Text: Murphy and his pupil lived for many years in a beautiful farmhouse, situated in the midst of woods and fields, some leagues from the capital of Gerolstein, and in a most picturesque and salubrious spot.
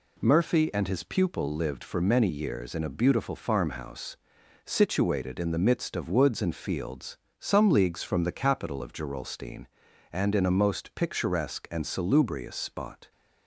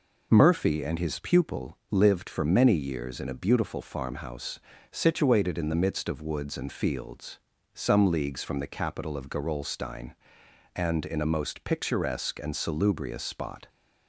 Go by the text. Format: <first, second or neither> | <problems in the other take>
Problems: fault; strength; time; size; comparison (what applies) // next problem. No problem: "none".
neither | none